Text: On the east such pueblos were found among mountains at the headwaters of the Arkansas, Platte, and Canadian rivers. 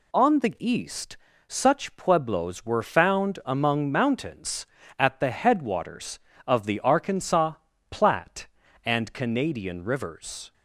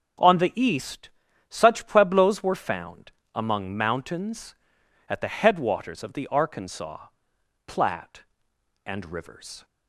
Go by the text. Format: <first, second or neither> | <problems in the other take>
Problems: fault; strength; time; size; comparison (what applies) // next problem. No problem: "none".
first | starts louder than the rest; strong; until 1.6 s; 8 dB // pauses between "east" and "such"; at 1.1 s; 0.38 s long; slight in the first // pauses between "found" and "among"; slight; at 3.1 s; 0.20 s long // skips "Canadian"; at 9.1 s